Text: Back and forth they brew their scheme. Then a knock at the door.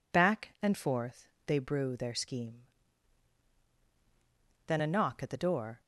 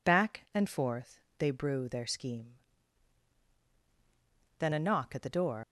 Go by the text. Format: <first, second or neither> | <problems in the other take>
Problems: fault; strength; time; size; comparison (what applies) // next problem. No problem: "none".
first | pauses between "forth" and "they"; slight; at 1.1 s; 0.20 s long; slight in the first // leaves "door" unfinished; at 5.6 s; 90 ms